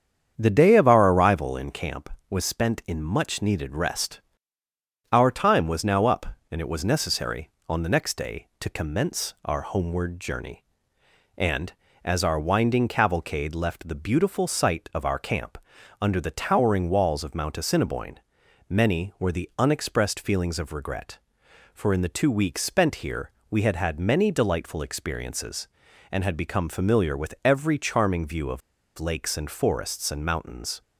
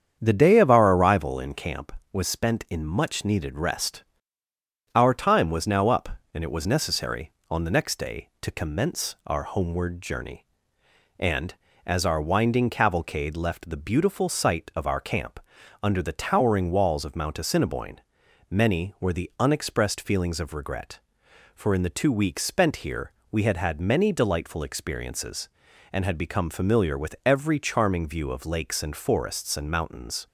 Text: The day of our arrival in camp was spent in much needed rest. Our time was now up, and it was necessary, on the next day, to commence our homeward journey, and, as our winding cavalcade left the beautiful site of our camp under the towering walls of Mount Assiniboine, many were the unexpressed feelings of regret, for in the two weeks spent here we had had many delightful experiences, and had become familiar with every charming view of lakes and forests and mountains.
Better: second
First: starts louder than the rest; strong; until 1.3 s; 8 dB // pauses between "camp" and "under"; at 15.5 s; 0.44 s long // pauses between "here" and "we"; slight; at 23.3 s; 0.18 s long // pauses between "of" and "lakes"; at 28.6 s; 0.38 s long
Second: starts louder than the rest; strong; until 1.2 s; 8 dB // pauses between "camp" and "under"; at 15.3 s; 0.44 s long // pauses between "here" and "we"; slight; at 23.1 s; 0.18 s long

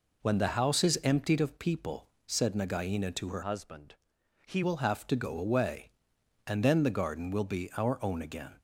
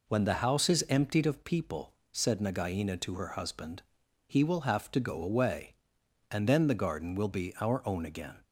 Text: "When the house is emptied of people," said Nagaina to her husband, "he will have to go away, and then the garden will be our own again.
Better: second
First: changes voice from "husband" to "he"; from 3.4 to 4.6 s; 1.2 s long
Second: none

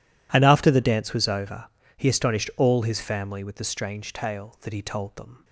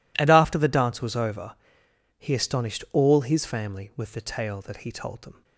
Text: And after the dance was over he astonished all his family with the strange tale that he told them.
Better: first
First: pauses between "over" and "he"; slight; at 1.6 s; 0.32 s long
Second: pauses between "over" and "he"; noticeable; at 1.5 s; 0.62 s long // skips "strange"; at 4.2 s

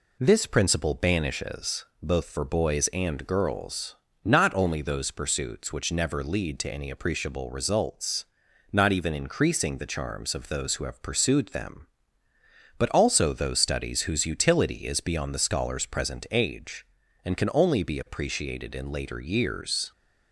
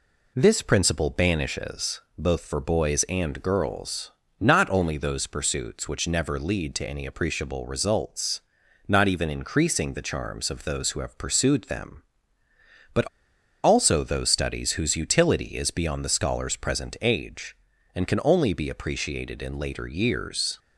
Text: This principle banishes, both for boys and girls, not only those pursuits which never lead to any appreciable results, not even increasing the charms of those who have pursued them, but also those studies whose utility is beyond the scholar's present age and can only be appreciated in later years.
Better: first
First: none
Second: pauses between "but" and "also"; noticeable; at 13.0 s; 0.57 s long

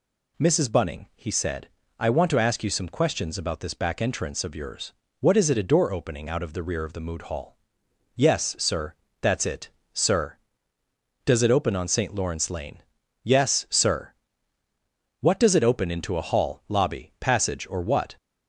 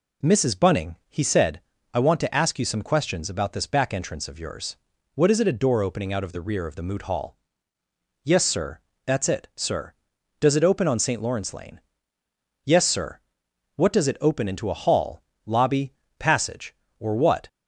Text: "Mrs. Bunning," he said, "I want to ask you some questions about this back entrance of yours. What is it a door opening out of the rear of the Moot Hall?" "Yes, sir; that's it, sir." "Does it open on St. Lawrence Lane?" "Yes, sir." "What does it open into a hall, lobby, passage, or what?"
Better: neither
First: none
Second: none

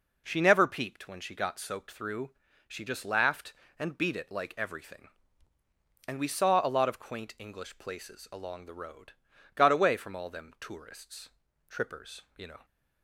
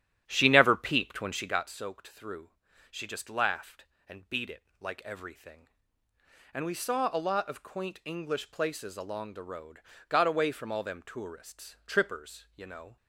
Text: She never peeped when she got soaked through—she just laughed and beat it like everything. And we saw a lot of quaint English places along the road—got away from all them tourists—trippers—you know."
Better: first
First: none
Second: starts louder than the rest; strong; until 1.7 s; 10.5 dB // pauses between "it" and "like"; slight; at 4.6 s; 0.18 s long

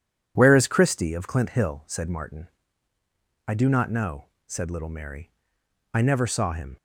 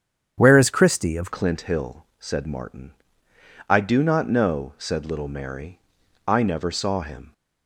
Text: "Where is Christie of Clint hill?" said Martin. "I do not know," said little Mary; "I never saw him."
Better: first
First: none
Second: starts louder than the rest; strong; until 1.3 s; 8 dB // changes voice at "Clint"; from 1.3 s on; 6.0 s long

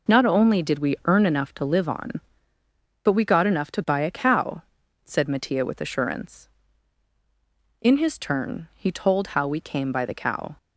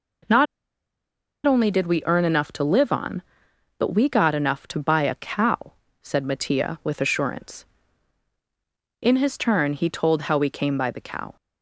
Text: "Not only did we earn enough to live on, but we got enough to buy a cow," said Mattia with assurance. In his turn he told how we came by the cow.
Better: first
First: none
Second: pauses between "Not" and "only"; at 0.4 s; 1.0 s long

